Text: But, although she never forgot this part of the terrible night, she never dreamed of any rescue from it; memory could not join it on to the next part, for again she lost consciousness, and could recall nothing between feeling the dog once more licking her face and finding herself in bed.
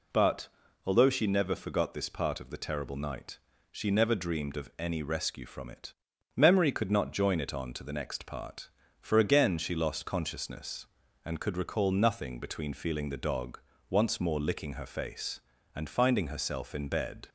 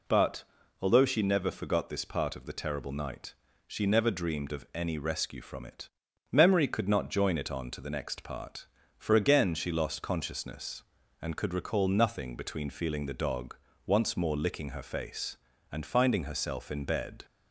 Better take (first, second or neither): neither